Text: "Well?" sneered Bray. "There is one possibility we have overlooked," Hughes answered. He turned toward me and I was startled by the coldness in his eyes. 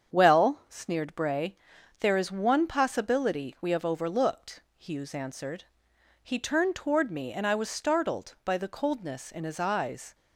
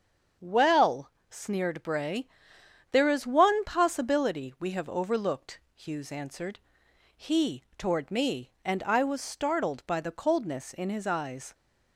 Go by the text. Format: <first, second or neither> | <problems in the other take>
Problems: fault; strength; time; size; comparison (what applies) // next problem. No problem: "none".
first | starts louder than the rest; until 1.6 s; 7 dB; strong in the first // skips "turned"; at 7.6 s